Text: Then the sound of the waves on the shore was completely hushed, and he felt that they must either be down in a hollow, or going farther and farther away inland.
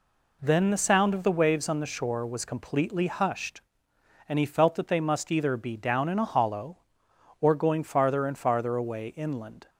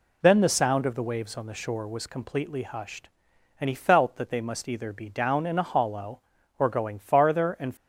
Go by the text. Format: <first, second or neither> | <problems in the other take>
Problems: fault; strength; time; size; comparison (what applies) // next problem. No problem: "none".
first | stops before "farther away inland"; at 7.7 s